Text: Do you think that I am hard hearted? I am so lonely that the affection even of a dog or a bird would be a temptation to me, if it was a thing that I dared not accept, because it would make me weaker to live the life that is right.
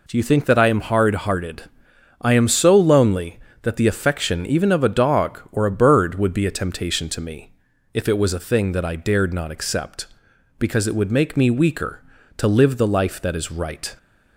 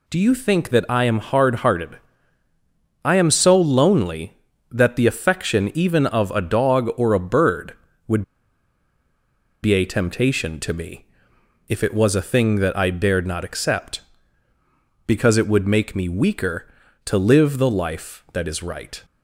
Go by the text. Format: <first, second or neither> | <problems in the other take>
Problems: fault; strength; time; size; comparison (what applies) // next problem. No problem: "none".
first | pauses between "would" and "be"; strong; at 8.2 s; 1.4 s long